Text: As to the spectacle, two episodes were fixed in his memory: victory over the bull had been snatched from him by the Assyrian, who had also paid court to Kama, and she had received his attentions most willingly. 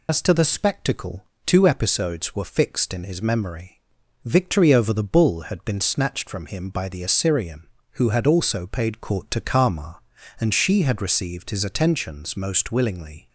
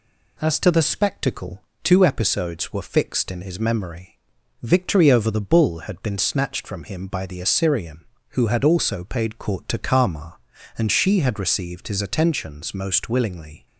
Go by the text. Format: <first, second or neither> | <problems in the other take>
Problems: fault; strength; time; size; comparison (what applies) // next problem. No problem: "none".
second | loses the start of "As"; at 0.0 s; 80 ms